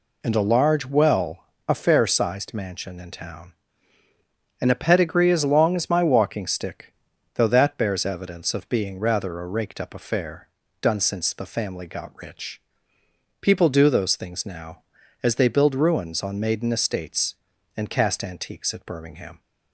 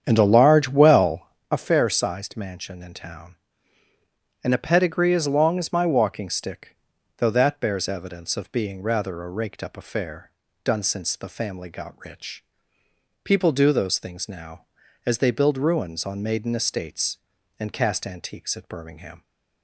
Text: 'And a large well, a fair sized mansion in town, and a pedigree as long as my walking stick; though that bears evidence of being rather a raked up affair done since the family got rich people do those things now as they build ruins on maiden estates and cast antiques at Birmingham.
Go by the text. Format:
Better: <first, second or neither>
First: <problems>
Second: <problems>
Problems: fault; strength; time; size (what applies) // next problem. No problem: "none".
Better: first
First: pauses between "affair" and "done"; slight; at 10.4 s; 0.34 s long // pauses between "rich" and "people"; noticeable; at 12.6 s; 0.80 s long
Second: starts louder than the rest; strong; until 1.5 s; 8.5 dB // pauses between "affair" and "done"; slight; at 10.2 s; 0.34 s long // pauses between "rich" and "people"; noticeable; at 12.4 s; 0.80 s long